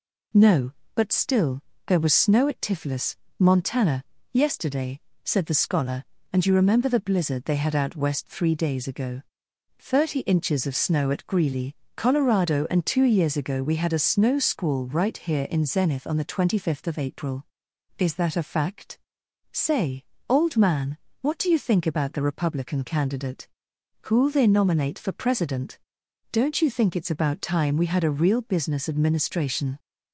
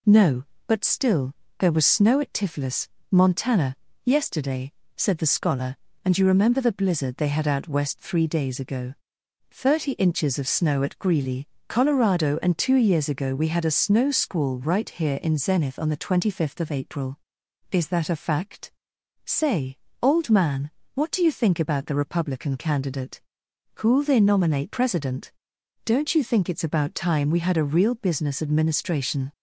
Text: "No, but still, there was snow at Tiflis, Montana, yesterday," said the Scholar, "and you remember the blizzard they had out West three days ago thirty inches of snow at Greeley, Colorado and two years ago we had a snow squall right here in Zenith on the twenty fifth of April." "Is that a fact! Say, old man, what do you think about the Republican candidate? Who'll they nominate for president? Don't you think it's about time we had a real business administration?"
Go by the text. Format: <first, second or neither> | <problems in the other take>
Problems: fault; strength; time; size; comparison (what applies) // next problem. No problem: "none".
first | pauses between "ago" and "thirty"; noticeable; at 8.9 s; 0.56 s long; noticeable in the first // skips "for"; at 24.6 s